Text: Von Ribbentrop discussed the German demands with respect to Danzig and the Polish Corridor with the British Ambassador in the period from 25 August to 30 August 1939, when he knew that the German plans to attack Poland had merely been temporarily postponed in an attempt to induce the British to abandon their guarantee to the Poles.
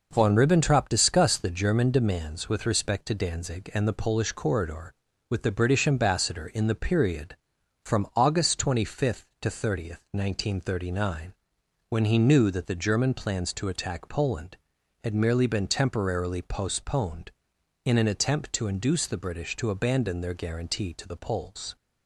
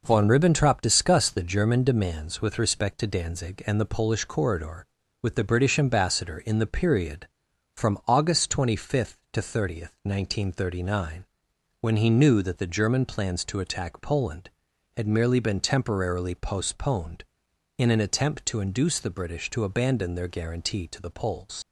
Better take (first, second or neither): first